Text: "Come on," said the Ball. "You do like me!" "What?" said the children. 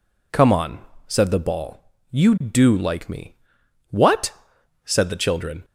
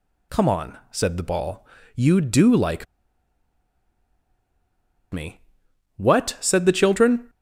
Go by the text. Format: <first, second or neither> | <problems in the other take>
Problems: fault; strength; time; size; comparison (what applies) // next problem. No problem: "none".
first | pauses between "like" and "me"; strong; at 2.8 s; 2.2 s long